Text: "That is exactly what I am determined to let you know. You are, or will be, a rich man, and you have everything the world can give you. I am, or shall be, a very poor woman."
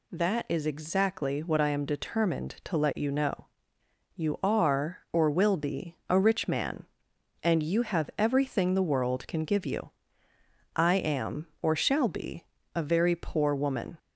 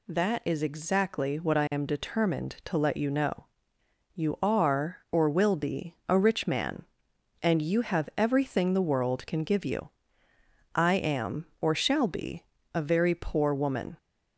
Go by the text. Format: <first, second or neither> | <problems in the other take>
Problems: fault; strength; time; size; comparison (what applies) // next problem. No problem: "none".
neither | none